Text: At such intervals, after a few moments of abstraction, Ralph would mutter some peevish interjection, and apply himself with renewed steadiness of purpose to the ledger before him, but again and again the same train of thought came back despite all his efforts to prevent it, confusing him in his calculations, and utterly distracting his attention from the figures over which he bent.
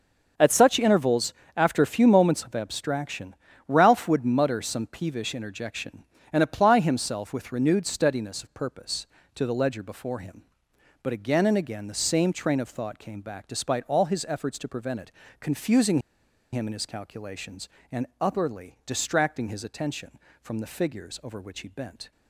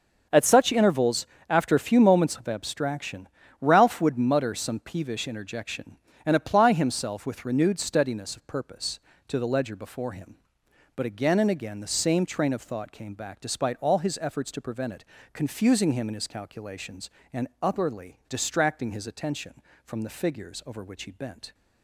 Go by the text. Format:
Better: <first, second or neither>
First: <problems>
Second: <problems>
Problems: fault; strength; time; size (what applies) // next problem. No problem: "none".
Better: second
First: starts louder than the rest; until 1.6 s; 6.5 dB // pauses between "confusing" and "him"; noticeable; at 15.9 s; 0.53 s long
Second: starts louder than the rest; until 1.5 s; 6.5 dB